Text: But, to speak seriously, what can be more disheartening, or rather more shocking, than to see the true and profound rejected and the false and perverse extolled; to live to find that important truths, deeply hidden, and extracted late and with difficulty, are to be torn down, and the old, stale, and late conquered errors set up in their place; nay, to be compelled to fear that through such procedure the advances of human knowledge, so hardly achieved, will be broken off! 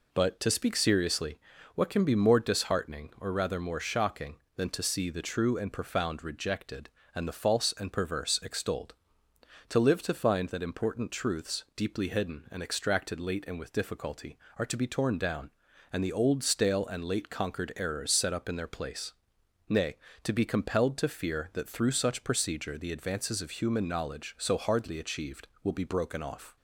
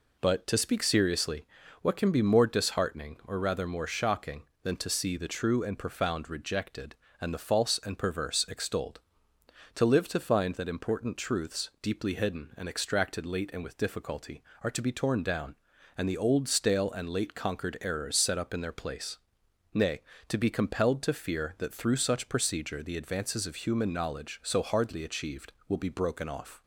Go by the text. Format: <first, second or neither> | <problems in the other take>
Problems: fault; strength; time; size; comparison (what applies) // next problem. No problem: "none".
neither | none